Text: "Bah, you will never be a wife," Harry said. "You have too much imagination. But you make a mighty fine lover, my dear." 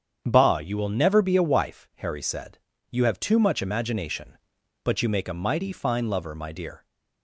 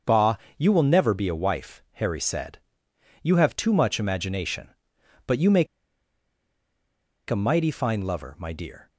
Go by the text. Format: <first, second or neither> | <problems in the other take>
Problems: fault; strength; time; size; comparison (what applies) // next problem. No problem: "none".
first | starts louder than the rest; until 1.2 s; 6.5 dB; strong in the first // pauses between "make" and "a"; strong; at 5.6 s; 1.6 s long